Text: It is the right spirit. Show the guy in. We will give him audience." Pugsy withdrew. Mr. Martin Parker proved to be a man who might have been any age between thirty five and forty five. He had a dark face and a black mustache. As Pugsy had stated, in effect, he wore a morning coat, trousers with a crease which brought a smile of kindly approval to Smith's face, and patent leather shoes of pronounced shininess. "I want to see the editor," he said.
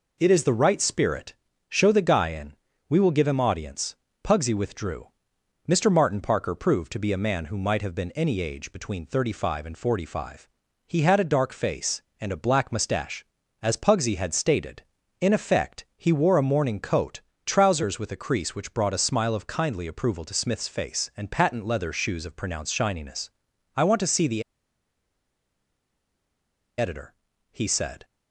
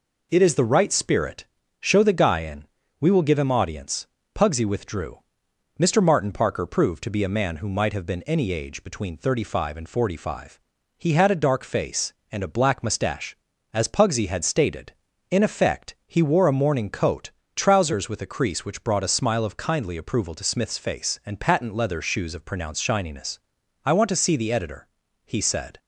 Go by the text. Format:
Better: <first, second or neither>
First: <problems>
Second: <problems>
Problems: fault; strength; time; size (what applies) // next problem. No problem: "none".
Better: second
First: pauses between "the" and "editor"; strong; at 24.4 s; 2.3 s long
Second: none